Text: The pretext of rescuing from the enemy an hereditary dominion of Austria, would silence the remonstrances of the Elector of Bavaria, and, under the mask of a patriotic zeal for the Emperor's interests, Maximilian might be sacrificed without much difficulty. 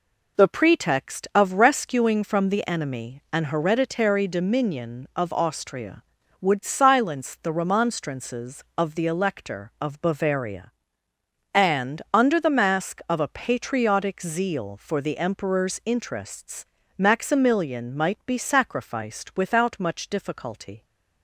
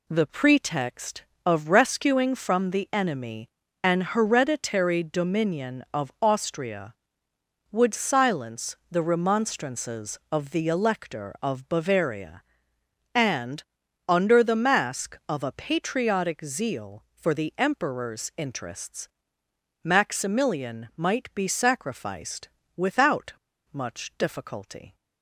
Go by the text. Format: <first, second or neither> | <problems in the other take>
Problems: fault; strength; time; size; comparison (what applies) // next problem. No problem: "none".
first | pauses between "enemy" and "an"; slight; at 3.4 s; 0.34 s long // pauses between "sacrificed" and "without"; slight; at 22.4 s; 0.26 s long // pauses between "without" and "much"; at 23.3 s; 0.39 s long